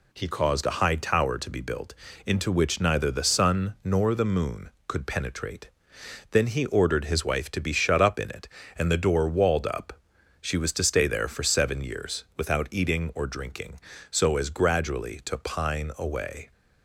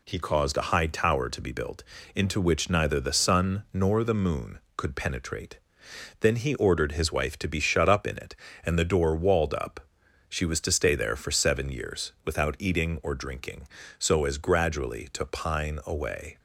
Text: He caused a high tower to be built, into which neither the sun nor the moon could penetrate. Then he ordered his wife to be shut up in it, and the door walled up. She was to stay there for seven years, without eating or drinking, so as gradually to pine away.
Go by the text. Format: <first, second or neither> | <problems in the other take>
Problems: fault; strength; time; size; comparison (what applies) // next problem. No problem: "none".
neither | none